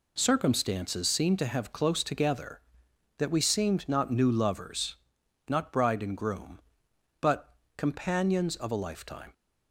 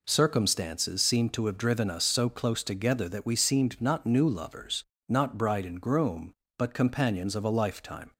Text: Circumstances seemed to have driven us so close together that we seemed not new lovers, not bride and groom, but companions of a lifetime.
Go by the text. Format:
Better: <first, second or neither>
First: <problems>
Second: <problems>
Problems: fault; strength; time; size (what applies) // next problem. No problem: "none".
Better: second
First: skips "driven us so"; at 1.7 s // pauses between "but" and "companions"; slight; at 7.5 s; 0.24 s long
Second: none